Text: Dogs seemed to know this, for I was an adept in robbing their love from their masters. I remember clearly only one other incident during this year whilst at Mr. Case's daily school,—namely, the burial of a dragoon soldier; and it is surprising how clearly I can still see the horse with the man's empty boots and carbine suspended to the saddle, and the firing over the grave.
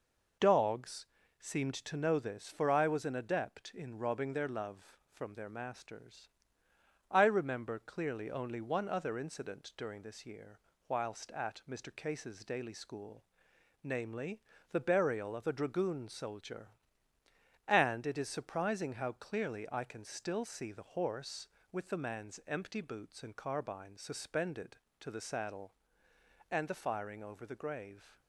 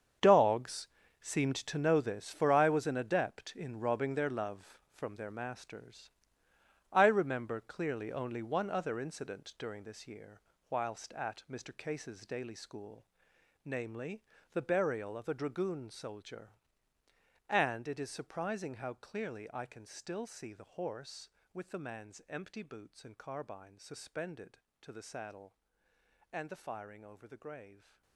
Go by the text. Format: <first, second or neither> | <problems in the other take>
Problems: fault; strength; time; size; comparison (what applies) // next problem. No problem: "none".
first | gets quieter; strong; throughout; 14 dB // pauses between "Dogs" and "seemed"; slight; at 0.8 s; 0.34 s long; slight in the first // pauses between "year" and "whilst"; slight; at 10.3 s; 0.30 s long; slight in the first